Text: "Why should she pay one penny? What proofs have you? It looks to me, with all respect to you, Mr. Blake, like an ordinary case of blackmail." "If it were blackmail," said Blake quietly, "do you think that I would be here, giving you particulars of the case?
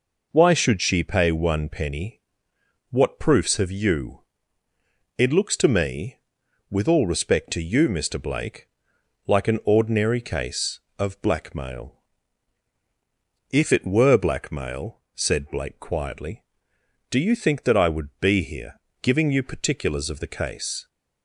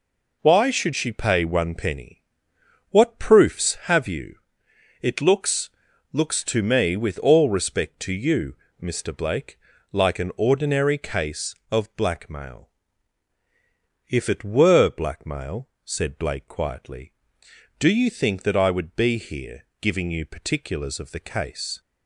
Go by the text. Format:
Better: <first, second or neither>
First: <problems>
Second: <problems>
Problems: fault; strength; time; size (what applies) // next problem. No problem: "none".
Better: first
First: none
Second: says "looks" twice; at 6.1 s